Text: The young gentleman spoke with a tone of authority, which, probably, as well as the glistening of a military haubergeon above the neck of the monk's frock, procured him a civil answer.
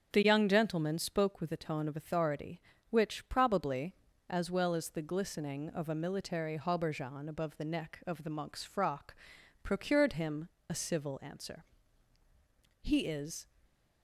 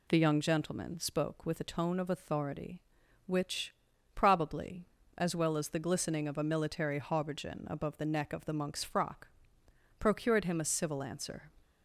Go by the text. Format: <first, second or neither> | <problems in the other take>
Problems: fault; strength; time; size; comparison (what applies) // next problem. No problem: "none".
second | starts louder than the rest; strong; until 1.1 s; 7.5 dB // pauses between "him" and "a"; slight; at 10.4 s; 0.18 s long // goes on to say "He is"; noticeable; from 12.8 s on; 0.64 s long